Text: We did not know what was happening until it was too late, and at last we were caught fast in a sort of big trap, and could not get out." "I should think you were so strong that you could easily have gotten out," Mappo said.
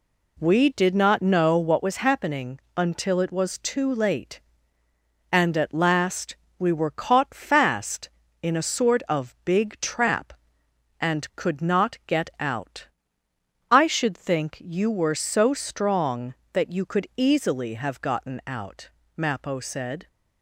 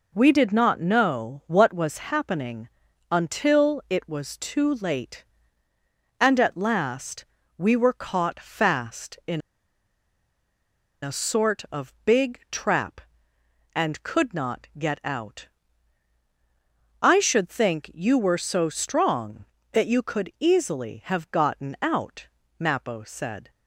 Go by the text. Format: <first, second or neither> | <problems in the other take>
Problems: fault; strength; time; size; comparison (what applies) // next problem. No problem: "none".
first | pauses between "happening" and "until"; at 2.6 s; 0.42 s long; slight in the first // pauses between "last" and "we"; slight; at 7.2 s; 0.32 s long; slight in the first // pauses between "in" and "a"; strong; at 9.4 s; 1.6 s long